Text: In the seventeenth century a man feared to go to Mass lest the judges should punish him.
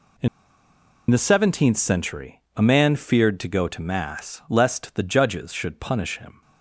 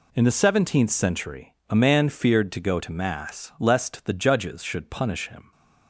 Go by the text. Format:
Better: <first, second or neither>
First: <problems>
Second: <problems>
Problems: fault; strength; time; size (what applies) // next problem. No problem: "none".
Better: second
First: pauses between "In" and "the"; noticeable; at 0.2 s; 0.82 s long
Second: none